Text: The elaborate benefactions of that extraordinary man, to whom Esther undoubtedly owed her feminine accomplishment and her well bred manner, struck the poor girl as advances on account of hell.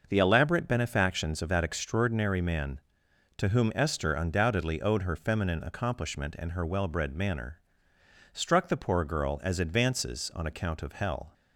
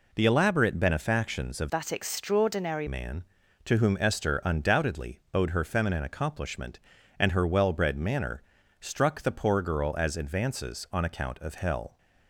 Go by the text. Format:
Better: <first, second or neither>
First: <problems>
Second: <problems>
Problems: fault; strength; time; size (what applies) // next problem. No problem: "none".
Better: first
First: none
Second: changes voice from "that" to "extraordinary"; from 1.6 to 2.8 s; 1.2 s long